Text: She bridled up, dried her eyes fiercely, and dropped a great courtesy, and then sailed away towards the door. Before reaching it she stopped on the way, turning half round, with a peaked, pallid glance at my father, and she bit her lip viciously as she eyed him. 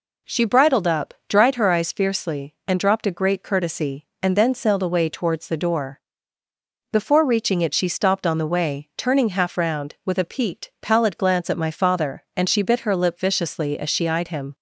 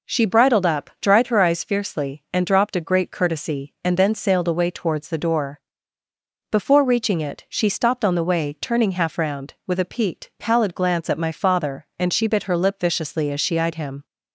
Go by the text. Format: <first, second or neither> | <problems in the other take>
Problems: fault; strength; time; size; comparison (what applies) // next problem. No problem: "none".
neither | none